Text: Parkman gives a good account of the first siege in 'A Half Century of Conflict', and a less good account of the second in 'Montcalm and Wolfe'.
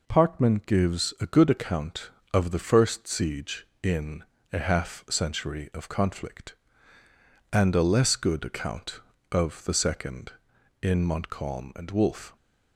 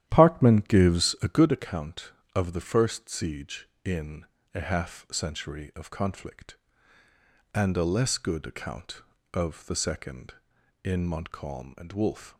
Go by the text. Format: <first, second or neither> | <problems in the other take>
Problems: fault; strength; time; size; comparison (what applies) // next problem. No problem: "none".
first | starts louder than the rest; strong; until 1.5 s; 11.5 dB // pauses between "in" and "A"; slight; at 4.2 s; 0.30 s long; slight in the first